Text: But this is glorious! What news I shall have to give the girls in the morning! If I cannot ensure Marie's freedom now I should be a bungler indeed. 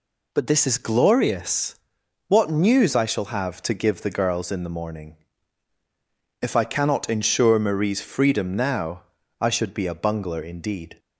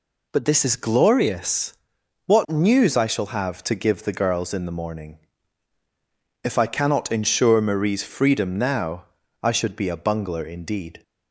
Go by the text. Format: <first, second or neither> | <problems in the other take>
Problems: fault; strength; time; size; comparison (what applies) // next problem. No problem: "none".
neither | pauses between "now" and "I"; the same in both